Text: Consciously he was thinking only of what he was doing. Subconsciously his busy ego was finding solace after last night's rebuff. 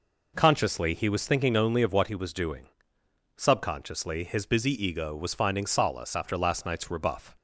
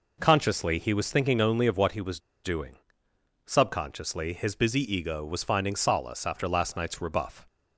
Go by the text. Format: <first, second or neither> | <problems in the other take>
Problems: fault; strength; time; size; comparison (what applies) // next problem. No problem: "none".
first | pauses between "was" and "doing"; slight; at 2.1 s; 0.24 s long